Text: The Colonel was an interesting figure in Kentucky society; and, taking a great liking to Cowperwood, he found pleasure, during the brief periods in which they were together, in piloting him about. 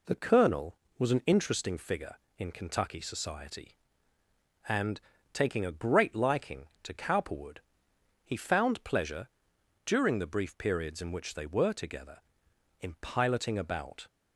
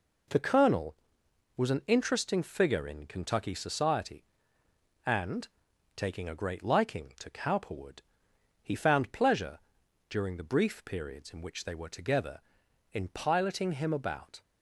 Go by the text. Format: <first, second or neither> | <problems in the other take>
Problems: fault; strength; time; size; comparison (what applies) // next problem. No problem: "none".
second | skips "him"; at 13.5 s